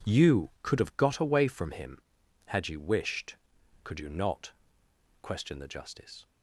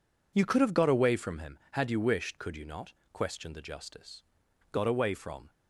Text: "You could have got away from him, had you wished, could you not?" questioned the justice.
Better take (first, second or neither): first